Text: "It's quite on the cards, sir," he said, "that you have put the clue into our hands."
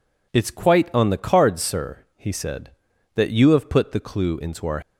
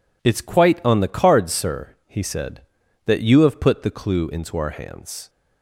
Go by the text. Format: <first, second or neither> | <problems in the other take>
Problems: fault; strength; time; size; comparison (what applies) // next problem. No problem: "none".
second | stops before "hands"; at 4.8 s